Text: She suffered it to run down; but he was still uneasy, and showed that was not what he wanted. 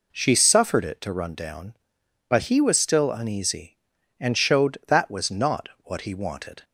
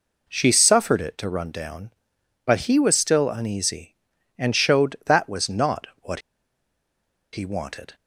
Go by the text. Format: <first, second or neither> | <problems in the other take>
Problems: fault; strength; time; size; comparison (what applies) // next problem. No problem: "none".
first | pauses between "not" and "what"; slight; at 5.8 s; 0.16 s long; slight in the first // pauses between "what" and "he"; at 6.2 s; 1.1 s long